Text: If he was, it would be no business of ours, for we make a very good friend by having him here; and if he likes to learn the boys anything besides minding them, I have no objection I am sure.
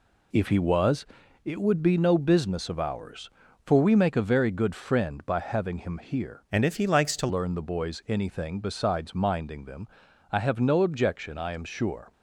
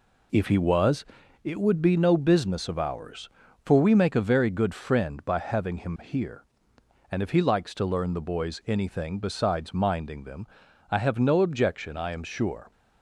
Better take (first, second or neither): second